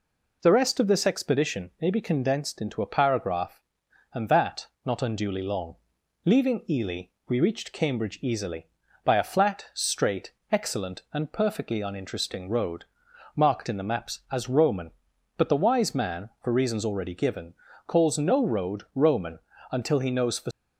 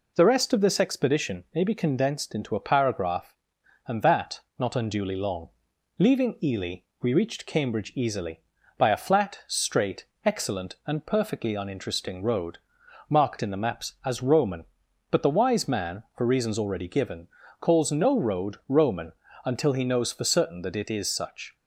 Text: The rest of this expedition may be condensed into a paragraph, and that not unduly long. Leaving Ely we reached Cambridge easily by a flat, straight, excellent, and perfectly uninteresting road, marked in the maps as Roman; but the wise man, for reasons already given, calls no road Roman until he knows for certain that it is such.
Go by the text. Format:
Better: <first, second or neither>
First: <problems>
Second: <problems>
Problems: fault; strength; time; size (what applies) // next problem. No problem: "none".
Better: second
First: pauses between "that" and "not"; slight; at 4.6 s; 0.18 s long // pauses between "Ely" and "we"; slight; at 7.0 s; 0.20 s long // pauses between "Roman" and "until"; slight; at 19.3 s; 0.32 s long // stops before "certain that it is such"; at 20.5 s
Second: pauses between "that" and "not"; slight; at 4.4 s; 0.18 s long // pauses between "Ely" and "we"; slight; at 6.8 s; 0.20 s long // pauses between "Roman" and "until"; slight; at 19.1 s; 0.32 s long